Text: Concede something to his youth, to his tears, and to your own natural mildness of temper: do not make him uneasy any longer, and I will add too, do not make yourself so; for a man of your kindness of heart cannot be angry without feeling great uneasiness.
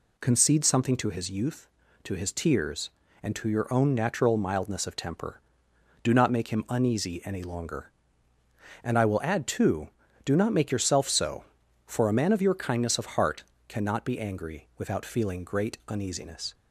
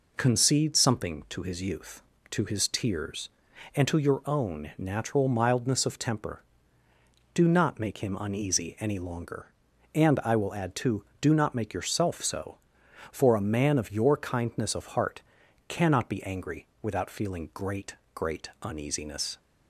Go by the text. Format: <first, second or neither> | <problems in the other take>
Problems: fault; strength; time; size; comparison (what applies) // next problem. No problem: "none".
first | pauses between "heart" and "cannot"; noticeable; at 15.2 s; 0.46 s long; slight in the first // pauses between "angry" and "without"; slight; at 16.6 s; 0.16 s long // says "great" twice; at 18.1 s